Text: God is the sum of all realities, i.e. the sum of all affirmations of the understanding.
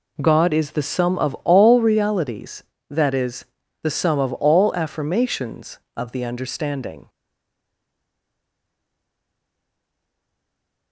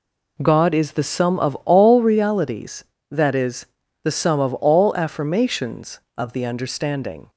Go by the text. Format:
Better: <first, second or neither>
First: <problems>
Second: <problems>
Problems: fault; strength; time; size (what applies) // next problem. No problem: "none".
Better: second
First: stays silent after the last word; strong; from 7.0 s on; 3.9 s long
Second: none